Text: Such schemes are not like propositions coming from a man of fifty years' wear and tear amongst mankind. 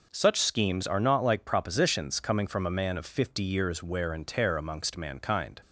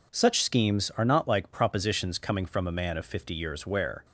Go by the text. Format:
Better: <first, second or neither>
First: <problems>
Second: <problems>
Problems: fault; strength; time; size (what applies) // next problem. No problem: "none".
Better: first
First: none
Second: stops before "and tear amongst mankind"; at 4.0 s